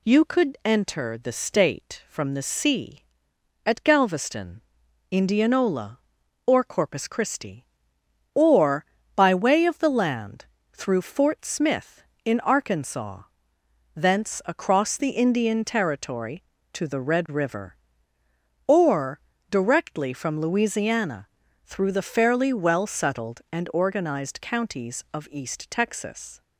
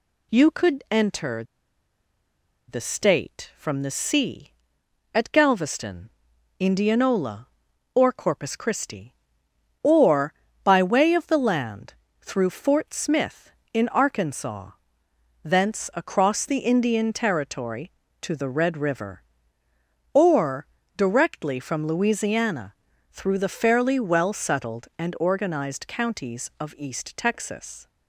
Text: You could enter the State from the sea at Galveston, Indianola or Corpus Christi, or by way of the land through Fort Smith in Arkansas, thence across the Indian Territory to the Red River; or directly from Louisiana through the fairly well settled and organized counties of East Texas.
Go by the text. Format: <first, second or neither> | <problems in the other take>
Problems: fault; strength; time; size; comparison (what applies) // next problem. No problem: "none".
first | pauses between "enter" and "the"; strong; at 1.4 s; 1.2 s long // pauses between "land" and "through"; slight; at 11.9 s; 0.28 s long; slight in the first // pauses between "or" and "directly"; slight; at 20.6 s; 0.28 s long; slight in the first // pauses between "Louisiana" and "through"; slight; at 22.7 s; 0.36 s long; slight in the first